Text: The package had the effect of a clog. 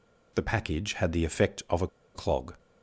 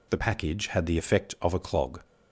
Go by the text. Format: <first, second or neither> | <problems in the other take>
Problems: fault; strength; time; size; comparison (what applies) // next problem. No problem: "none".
second | pauses between "a" and "clog"; slight; at 1.8 s; 0.28 s long